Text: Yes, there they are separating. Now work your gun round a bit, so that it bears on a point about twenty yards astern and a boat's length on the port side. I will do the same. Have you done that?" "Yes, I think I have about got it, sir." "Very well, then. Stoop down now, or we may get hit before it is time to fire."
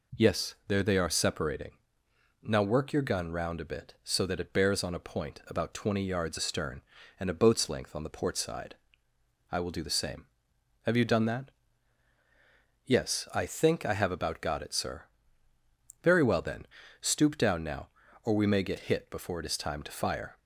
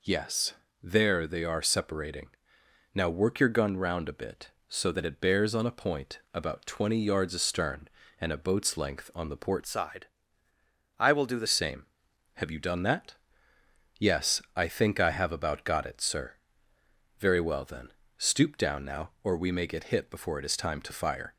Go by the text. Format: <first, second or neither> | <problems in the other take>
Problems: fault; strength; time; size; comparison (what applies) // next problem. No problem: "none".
first | changes voice from "side" to "the"; from 9.6 to 11.4 s; 1.8 s long